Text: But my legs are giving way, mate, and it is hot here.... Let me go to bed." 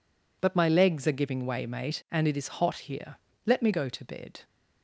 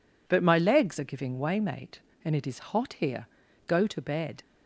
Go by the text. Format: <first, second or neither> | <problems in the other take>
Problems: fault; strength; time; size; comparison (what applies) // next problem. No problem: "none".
first | skips "Let me"; at 3.4 s